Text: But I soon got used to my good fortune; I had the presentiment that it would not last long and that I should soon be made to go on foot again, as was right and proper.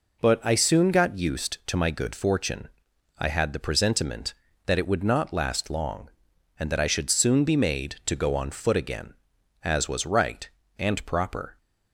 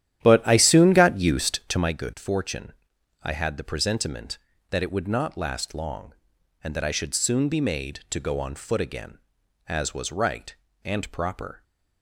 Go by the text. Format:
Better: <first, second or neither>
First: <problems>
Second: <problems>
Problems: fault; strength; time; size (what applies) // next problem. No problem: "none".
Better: first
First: none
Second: starts louder than the rest; strong; until 2.0 s; 11 dB